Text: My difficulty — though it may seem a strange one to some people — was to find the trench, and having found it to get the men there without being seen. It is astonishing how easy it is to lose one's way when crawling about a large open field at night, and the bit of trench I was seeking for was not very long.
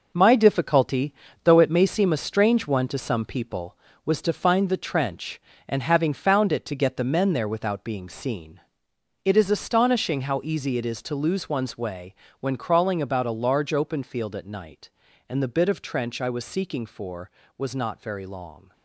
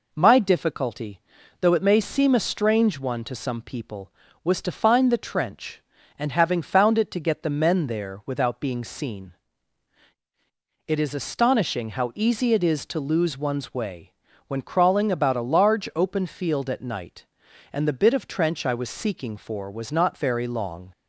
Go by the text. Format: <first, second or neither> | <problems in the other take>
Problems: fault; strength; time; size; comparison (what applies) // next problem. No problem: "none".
second | gets quieter; strong; throughout; 8.5 dB // pauses between "way" and "when"; slight; at 12.1 s; 0.26 s long; slight in the second